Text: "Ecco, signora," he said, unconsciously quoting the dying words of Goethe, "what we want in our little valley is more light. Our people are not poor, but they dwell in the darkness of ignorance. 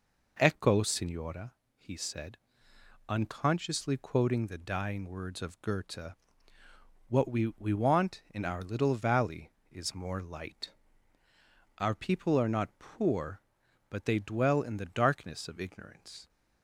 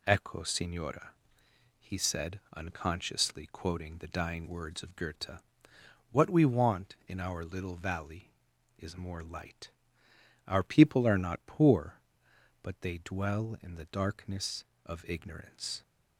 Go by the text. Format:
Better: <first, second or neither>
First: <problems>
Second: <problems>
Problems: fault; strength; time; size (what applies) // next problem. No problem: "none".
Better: second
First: says "we" twice; at 7.5 s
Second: none